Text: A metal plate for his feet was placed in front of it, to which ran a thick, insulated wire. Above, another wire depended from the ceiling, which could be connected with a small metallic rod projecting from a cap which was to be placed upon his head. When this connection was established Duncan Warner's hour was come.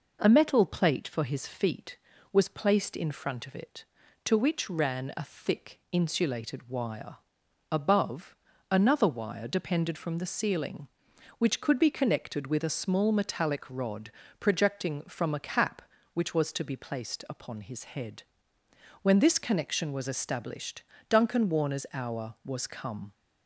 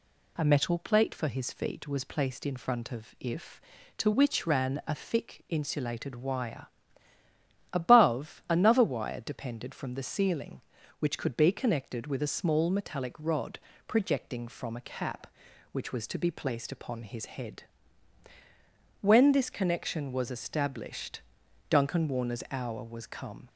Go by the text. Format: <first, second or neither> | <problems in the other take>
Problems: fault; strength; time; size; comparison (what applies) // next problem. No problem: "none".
first | says "if" for "it"; at 3.1 s // pauses between "rod" and "projecting"; slight; at 13.5 s; 0.30 s long; slight in the first // pauses between "established" and "Duncan"; noticeable; at 21.2 s; 0.48 s long; slight in the first